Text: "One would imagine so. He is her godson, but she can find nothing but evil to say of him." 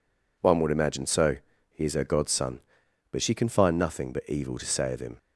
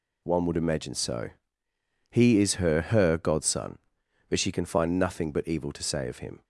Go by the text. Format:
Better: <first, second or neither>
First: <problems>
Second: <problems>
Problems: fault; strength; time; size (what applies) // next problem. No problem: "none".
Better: first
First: none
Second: says "her" twice; at 2.8 s